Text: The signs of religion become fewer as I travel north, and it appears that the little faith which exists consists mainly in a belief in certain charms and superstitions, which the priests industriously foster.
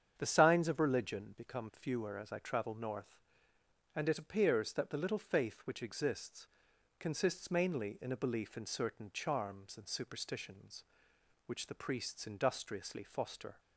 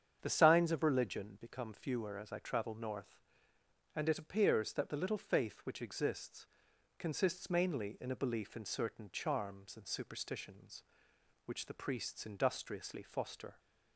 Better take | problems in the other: neither | starts louder than the rest; strong; the same in both // pauses between "exists" and "consists"; noticeable; the same in both

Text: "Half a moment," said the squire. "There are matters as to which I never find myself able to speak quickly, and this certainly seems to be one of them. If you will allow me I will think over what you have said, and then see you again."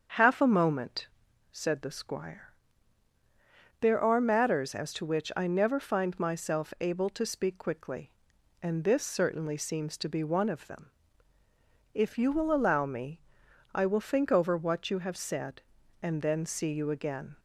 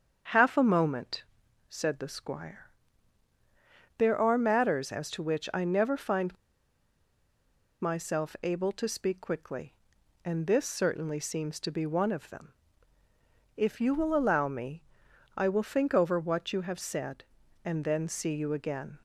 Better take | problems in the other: first | starts louder than the rest; until 1.7 s; 7 dB; also in the first // pauses between "find" and "myself"; strong; at 6.3 s; 1.4 s long // pauses between "me" and "I"; noticeable; at 14.8 s; 0.54 s long; noticeable in the first

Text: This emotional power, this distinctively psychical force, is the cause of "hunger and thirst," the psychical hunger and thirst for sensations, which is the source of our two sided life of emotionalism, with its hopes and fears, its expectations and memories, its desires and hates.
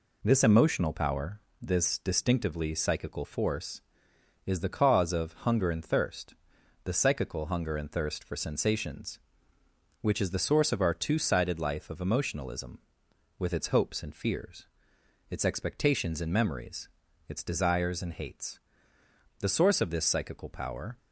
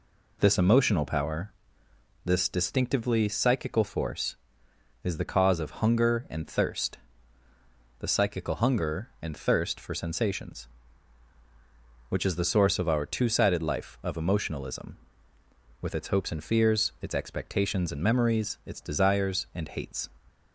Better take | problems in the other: second | goes on to say "The source of this psychical power"; from 19.3 s on; 1.5 s long

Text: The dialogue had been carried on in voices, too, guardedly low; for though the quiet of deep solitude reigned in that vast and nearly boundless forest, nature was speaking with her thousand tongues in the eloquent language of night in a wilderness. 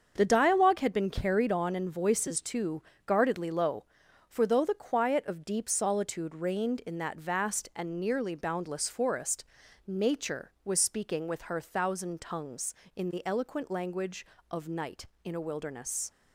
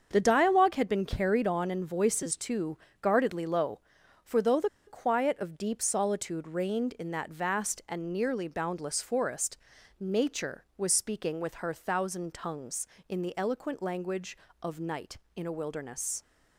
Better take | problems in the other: first | starts louder than the rest; until 1.1 s; 7 dB; also in the first // pauses between "the" and "quiet"; slight; at 4.6 s; 0.19 s long

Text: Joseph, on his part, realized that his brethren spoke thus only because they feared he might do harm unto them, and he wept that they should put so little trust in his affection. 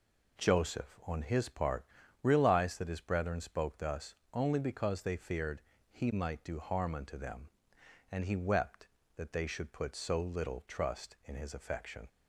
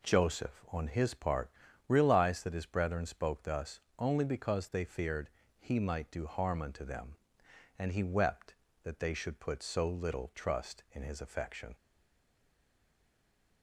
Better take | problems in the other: first | pauses between "thus" and "only"; slight; at 3.7 s; 0.20 s long; slight in the first // pauses between "feared" and "he"; slight; at 5.2 s; 0.30 s long; slight in the first // stays silent after the last word; noticeable; from 11.7 s on; 1.9 s long

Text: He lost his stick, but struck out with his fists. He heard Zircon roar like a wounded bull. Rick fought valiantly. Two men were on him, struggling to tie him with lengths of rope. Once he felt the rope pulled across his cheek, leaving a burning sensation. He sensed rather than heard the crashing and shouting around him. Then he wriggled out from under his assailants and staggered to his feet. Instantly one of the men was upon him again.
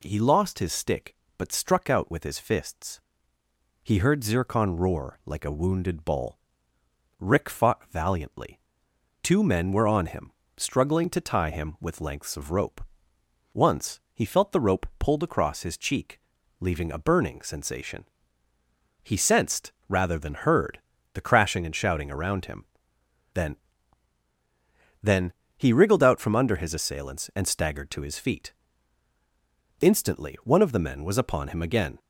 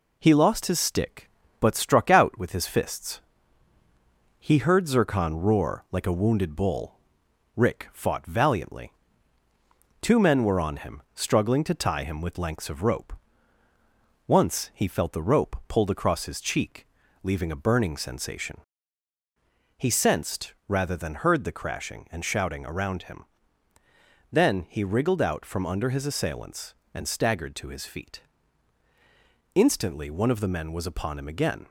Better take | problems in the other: second | pauses between "sensed" and "rather"; slight; at 19.7 s; 0.16 s long // pauses between "heard" and "the"; slight; at 20.7 s; 0.36 s long // says "Then" twice; at 25.0 s

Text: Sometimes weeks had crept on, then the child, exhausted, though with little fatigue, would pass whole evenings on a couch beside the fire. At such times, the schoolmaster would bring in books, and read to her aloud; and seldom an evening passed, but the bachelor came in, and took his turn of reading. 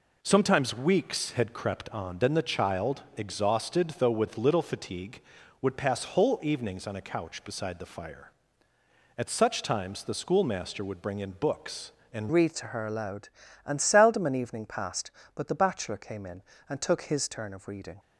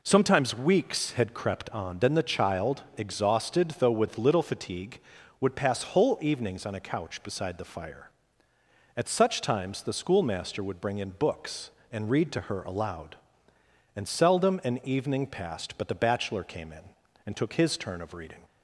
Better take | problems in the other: second | changes voice at "read"; from 12.3 s on; 5.6 s long

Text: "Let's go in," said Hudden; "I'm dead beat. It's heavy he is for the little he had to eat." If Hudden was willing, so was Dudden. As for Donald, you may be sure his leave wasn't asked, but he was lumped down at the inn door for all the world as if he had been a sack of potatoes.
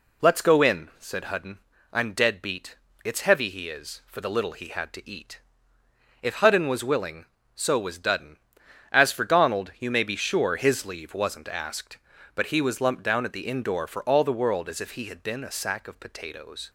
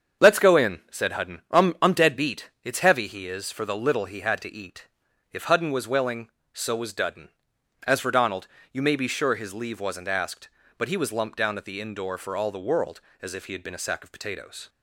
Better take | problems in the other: first | starts louder than the rest; strong; until 1.3 s; 7 dB // says "I'm" twice; at 1.8 s

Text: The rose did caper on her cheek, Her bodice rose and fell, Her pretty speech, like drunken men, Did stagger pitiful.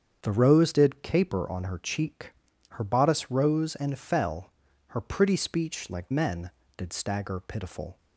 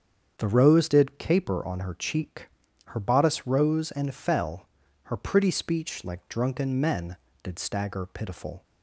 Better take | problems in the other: second | starts louder than the rest; strong; until 1.2 s; 7.5 dB; strong in the second // skips "drunken"; at 6.1 s

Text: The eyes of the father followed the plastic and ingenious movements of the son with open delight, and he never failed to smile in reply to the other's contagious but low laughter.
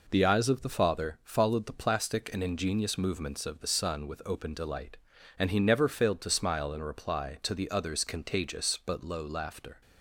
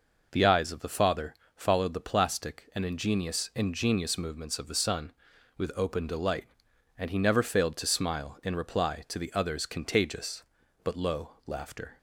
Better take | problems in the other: first | pauses between "father" and "followed"; slight; at 1.3 s; 0.22 s long // says "ingenious" twice; at 3.5 s

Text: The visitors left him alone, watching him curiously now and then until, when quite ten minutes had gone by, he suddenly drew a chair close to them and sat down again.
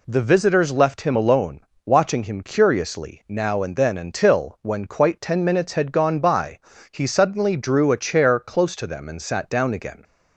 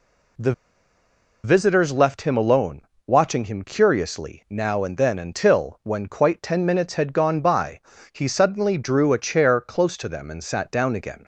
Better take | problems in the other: first | pauses between "The" and "visitors"; noticeable; at 0.5 s; 0.92 s long

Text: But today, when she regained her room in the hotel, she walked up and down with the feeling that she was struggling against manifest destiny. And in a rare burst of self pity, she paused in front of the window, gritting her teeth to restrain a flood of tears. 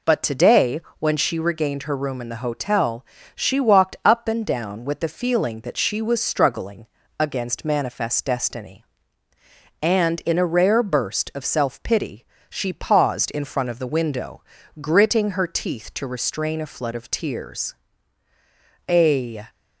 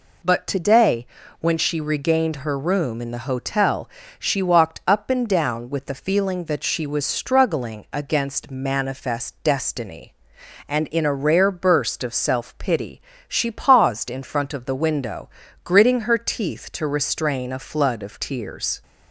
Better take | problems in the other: second | pauses between "struggling" and "against"; slight; at 6.8 s; 0.32 s long // goes on to say "A"; from 18.8 s on; 0.58 s long

